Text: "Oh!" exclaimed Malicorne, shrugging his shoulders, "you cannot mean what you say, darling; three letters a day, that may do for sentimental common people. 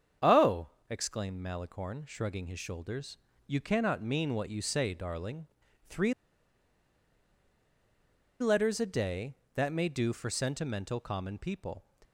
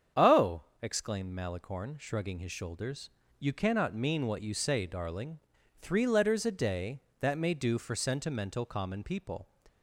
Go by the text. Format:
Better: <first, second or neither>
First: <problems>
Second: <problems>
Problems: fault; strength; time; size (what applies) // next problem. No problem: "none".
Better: second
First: starts louder than the rest; strong; until 1.4 s; 8 dB // pauses between "three" and "letters"; strong; at 6.1 s; 2.2 s long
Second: starts louder than the rest; strong; until 1.3 s; 7.5 dB